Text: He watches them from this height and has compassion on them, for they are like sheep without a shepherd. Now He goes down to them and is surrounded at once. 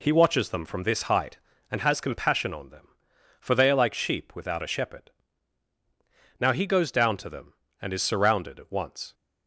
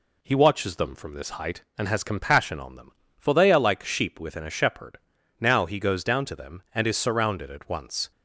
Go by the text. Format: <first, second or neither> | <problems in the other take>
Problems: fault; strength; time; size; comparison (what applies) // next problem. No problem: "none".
first | says "within" for "without"; at 4.1 s